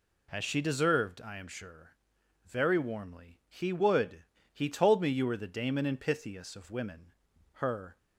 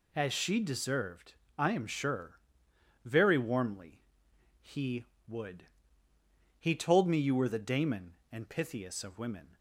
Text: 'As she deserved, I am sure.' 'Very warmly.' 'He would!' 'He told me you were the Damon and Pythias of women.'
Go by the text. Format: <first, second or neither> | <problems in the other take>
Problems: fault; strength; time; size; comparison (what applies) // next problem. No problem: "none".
second | goes on to say "Her"; slight; from 7.5 s on; 0.44 s long